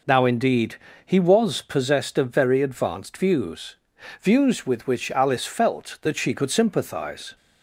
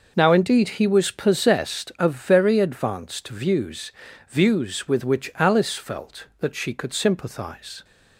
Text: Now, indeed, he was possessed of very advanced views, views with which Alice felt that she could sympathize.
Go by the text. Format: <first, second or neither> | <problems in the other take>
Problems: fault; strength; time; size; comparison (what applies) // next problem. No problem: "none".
neither | none